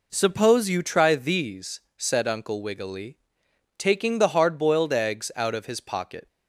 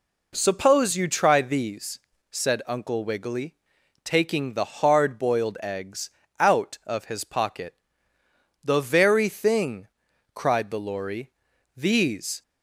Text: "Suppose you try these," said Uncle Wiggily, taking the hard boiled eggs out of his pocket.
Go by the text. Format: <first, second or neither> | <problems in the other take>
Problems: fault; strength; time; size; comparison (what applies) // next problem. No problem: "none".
first | pauses between "eggs" and "out"; slight; at 6.0 s; 0.30 s long // goes on to say "The very thing cried the Lory These"; strong; from 8.6 s on; 3.7 s long